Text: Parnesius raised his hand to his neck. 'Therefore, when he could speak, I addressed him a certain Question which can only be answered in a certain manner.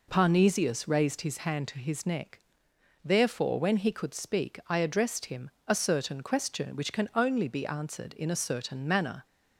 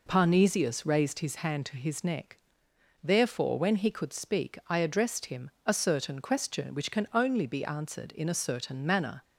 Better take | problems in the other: neither | pauses between "him" and "a"; slight; the same in both

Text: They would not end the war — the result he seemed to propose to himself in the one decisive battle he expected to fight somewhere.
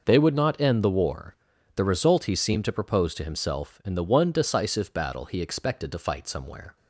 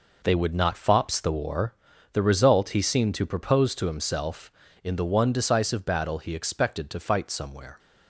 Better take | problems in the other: first | says "fops" for "end"; at 0.7 s

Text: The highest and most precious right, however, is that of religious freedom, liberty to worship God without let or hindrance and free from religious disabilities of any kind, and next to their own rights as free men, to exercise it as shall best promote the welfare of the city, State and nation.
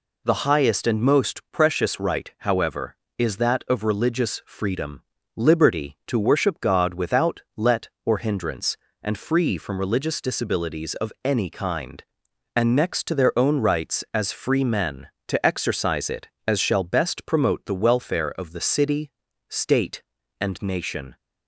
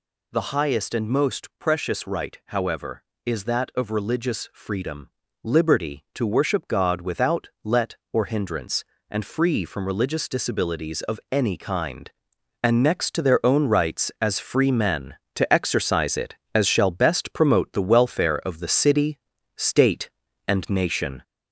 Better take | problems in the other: first | gets louder; slight; throughout; 2.5 dB

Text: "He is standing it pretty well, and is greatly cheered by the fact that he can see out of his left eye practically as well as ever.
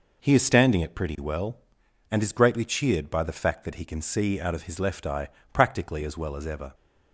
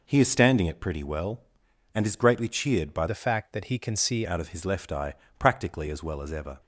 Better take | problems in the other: first | changes voice from "the" to "see"; from 3.0 to 4.2 s; 1.2 s long // pauses between "eye" and "practically"; slight; at 5.1 s; 0.22 s long; slight in the first

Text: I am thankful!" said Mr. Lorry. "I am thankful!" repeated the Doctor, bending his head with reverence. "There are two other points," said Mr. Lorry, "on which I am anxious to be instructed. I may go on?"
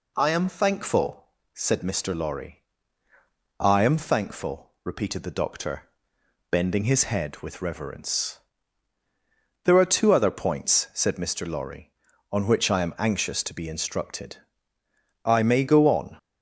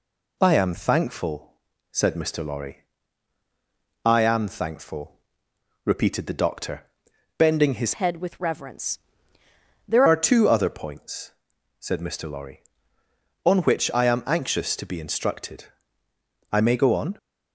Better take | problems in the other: first | changes voice from "head" to "There"; from 7.9 to 10.0 s; 2.1 s long

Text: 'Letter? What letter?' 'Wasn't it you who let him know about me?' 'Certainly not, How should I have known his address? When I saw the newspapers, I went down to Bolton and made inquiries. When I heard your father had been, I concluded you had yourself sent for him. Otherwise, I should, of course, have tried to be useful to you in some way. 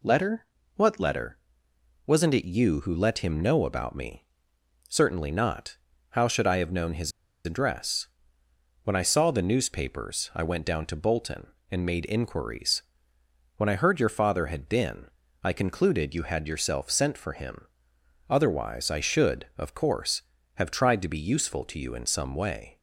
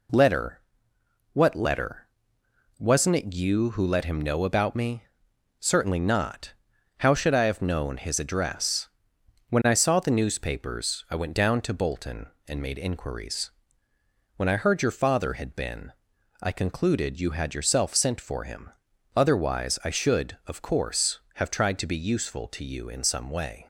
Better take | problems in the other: second | pauses between "his" and "address"; slight; at 7.1 s; 0.34 s long

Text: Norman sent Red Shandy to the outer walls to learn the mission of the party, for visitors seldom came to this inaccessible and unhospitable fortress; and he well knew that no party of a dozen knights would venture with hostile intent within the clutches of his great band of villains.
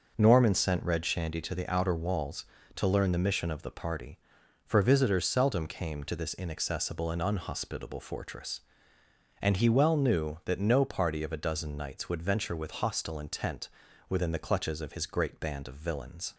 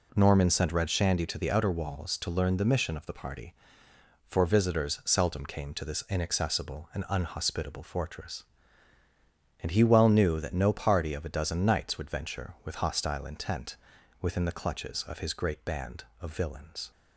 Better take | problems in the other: neither | pauses between "intent" and "within"; the same in both

